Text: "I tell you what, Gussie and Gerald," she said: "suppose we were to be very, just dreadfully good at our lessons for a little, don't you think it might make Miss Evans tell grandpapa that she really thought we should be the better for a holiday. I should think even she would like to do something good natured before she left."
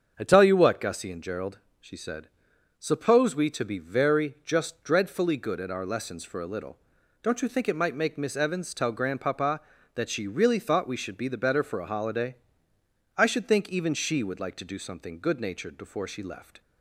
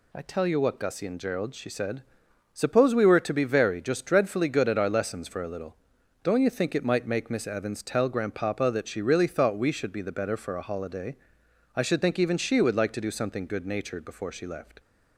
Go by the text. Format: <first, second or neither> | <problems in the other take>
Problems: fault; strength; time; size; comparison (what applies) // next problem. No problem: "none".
second | starts louder than the rest; strong; until 1.1 s; 7.5 dB // skips "were"; at 3.4 s